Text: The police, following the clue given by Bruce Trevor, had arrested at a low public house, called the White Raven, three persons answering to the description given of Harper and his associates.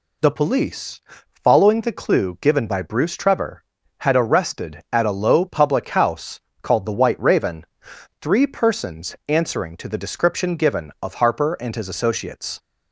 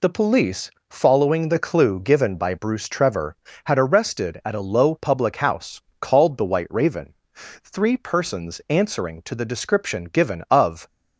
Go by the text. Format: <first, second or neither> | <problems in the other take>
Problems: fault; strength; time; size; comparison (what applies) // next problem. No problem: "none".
first | stops before "Harper and his associates"; at 10.8 s